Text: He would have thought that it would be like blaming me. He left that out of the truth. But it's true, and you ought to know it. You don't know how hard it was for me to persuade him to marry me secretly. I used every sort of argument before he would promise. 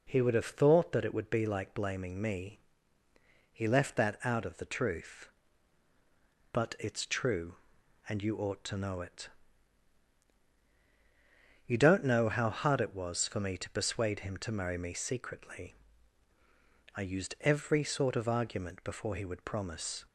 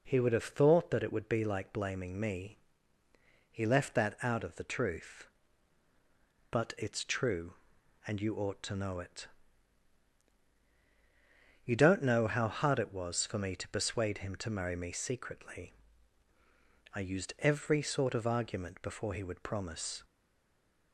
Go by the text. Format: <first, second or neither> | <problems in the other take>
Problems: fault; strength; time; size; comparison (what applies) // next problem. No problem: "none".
first | stays silent after the last word; slight; from 20.0 s on; 0.9 s long